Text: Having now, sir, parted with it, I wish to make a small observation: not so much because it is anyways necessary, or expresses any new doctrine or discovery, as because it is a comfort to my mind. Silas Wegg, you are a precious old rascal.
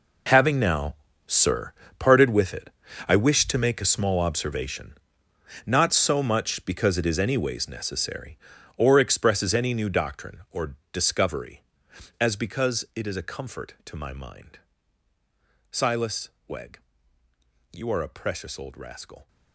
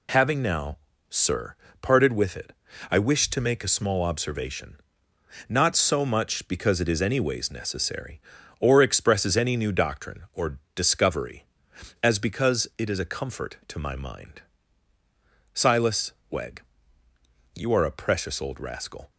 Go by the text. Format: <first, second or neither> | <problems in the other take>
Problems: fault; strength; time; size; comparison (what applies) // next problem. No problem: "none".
second | gets quieter; strong; throughout; 15 dB // pauses between "or" and "discovery"; slight; at 10.7 s; 0.16 s long; slight in the second // pauses between "Silas" and "Wegg"; slight; at 16.2 s; 0.18 s long; slight in the second